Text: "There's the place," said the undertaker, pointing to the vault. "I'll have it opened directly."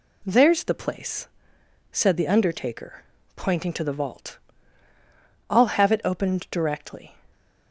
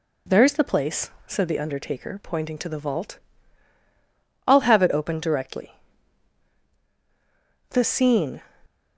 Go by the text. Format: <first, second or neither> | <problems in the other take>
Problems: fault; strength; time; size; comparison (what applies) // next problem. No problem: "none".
first | goes on to say "The scene"; noticeable; from 7.6 s on; 0.72 s long